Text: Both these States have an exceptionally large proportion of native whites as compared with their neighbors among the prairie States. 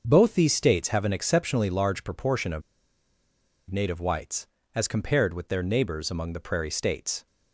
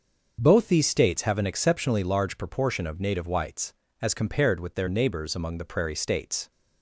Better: second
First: starts louder than the rest; until 1.0 s; 6.5 dB // pauses between "of" and "native"; at 2.6 s; 1.0 s long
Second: starts louder than the rest; until 1.4 s; 6.5 dB

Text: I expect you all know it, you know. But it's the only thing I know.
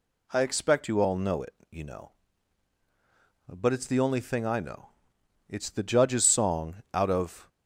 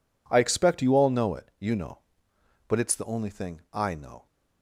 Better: second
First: goes on to say "It's the Judge's song out of"; strong; from 5.4 s on; 2.0 s long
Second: none

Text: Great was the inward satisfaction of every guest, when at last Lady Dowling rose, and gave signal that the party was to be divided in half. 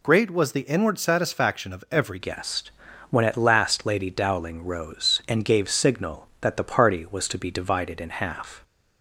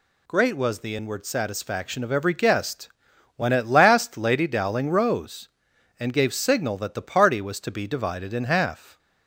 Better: second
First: changes voice at "guest"; from 2.1 s on; 6.5 s long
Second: none

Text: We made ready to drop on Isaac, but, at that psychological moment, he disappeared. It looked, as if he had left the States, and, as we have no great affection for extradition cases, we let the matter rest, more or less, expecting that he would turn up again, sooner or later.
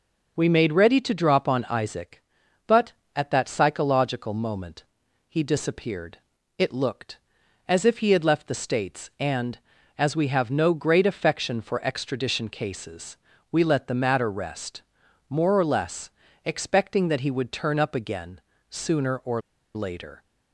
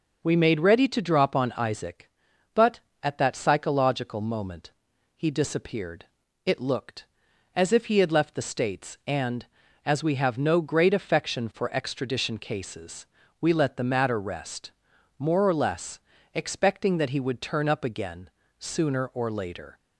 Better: second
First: pauses between "or" and "later"; slight; at 19.3 s; 0.35 s long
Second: none

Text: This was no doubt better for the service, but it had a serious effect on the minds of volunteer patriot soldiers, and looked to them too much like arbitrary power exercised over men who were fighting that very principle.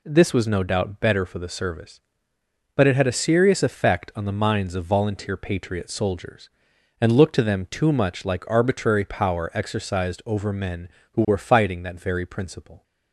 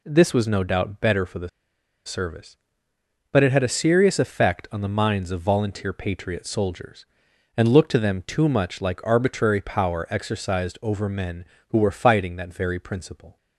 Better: first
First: none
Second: pauses between "the" and "service"; noticeable; at 1.4 s; 0.57 s long

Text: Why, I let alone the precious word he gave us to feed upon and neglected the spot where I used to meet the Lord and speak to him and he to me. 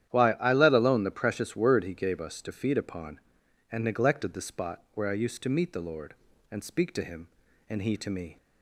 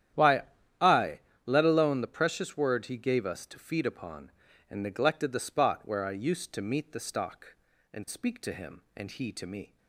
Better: first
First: starts louder than the rest; strong; until 1.1 s; 10.5 dB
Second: starts louder than the rest; strong; until 1.7 s; 10.5 dB // pauses between "I" and "let"; slight; at 1.1 s; 0.26 s long // says "Stock" for "Lord"; at 6.9 s

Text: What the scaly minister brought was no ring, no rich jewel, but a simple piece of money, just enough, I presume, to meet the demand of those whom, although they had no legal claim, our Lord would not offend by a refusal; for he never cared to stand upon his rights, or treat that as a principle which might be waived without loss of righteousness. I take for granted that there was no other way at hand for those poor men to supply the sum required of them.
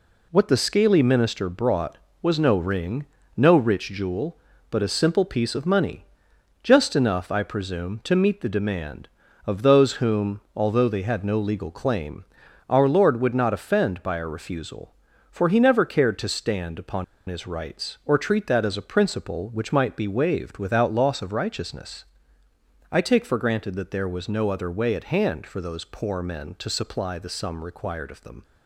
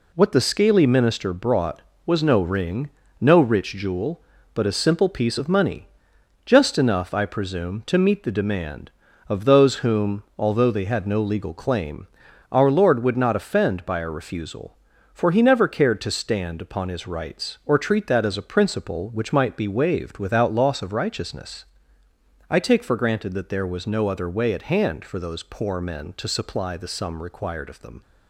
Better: second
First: pauses between "upon" and "his"; slight; at 17.0 s; 0.24 s long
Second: none

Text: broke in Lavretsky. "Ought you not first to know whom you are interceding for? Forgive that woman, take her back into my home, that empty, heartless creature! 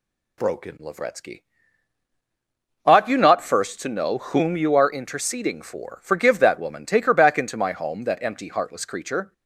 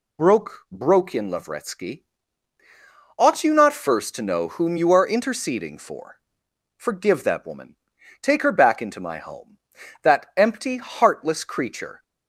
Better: first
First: none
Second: says "broke" twice; at 0.6 s

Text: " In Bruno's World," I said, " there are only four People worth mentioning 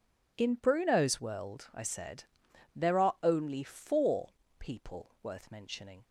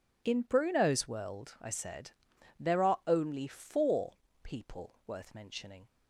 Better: neither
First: pauses between "four" and "People"; slight; at 4.2 s; 0.30 s long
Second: pauses between "four" and "People"; slight; at 4.1 s; 0.30 s long

